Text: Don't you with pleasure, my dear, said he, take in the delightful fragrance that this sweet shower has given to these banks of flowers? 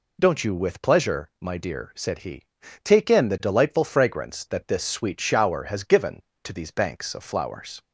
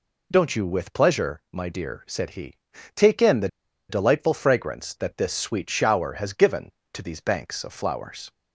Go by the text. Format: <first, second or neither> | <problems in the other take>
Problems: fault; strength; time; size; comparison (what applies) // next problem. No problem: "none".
first | pauses between "the" and "delightful"; at 3.4 s; 0.42 s long